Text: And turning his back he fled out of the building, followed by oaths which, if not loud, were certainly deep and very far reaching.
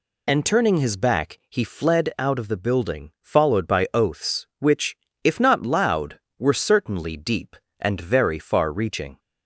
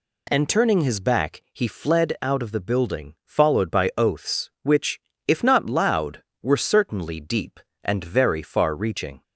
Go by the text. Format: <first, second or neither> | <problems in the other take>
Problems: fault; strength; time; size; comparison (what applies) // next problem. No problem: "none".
second | loses the start of "And"; at 0.2 s; 40 ms